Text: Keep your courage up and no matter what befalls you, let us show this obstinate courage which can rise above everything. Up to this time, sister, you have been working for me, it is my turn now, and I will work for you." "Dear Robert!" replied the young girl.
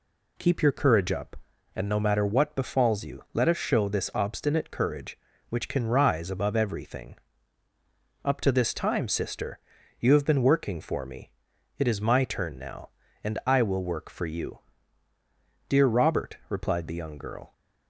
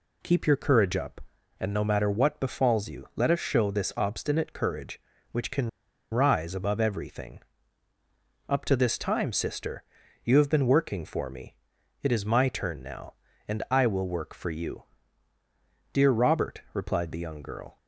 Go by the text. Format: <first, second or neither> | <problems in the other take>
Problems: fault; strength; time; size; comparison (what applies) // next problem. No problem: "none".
first | pauses between "can" and "rise"; at 5.6 s; 0.43 s long